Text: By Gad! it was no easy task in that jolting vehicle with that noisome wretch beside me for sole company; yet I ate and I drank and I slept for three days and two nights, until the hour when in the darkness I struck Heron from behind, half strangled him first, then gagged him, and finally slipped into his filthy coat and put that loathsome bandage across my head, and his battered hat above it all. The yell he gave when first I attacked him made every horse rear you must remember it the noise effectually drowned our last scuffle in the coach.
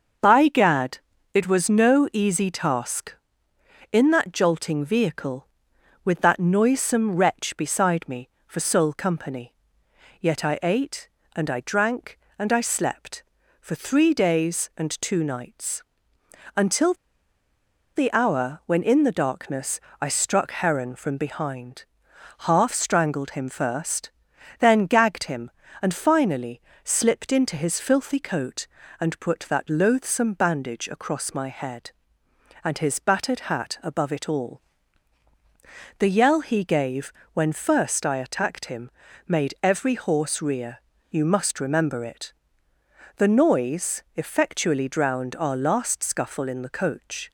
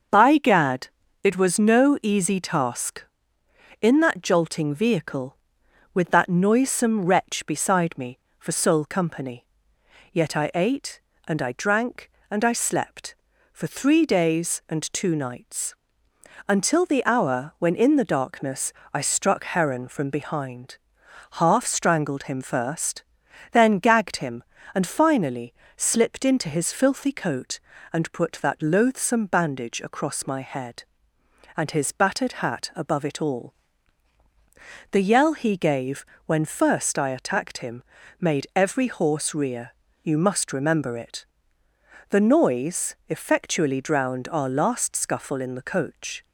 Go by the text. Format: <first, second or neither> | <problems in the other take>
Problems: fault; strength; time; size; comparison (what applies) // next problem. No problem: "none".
second | starts louder than the rest; until 1.5 s; 6.5 dB; also in the second // pauses between "until" and "the"; at 16.9 s; 1.0 s long // pauses between "darkness" and "I"; slight; at 19.7 s; 0.22 s long; slight in the second // pauses between "finally" and "slipped"; slight; at 26.6 s; 0.22 s long; slight in the second // pauses between "gave" and "when"; slight; at 37.1 s; 0.22 s long; slight in the second // pauses between "him" and "made"; slight; at 38.9 s; 0.36 s long; slight in the second // pauses between "rear" and "you"; slight; at 40.7 s; 0.30 s long; slight in the second // pauses between "it" and "the"; noticeable; at 42.3 s; 0.86 s long; noticeable in the second